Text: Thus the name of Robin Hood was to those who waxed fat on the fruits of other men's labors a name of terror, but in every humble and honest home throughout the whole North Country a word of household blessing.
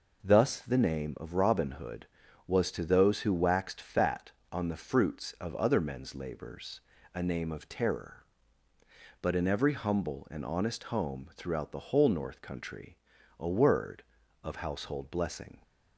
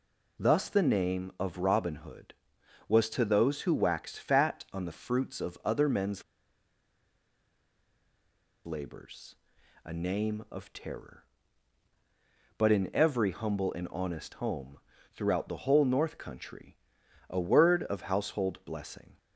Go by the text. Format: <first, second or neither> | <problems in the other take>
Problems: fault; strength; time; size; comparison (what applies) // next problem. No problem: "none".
first | pauses between "men's" and "labors"; strong; at 6.2 s; 2.4 s long // pauses between "labors" and "a"; noticeable; at 9.3 s; 0.48 s long; slight in the first // pauses between "home" and "throughout"; slight; at 14.7 s; 0.34 s long // pauses between "Country" and "a"; noticeable; at 16.7 s; 0.52 s long; also in the first